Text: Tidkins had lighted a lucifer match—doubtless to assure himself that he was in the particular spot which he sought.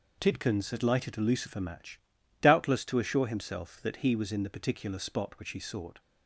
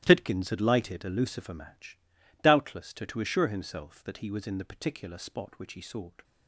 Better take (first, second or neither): first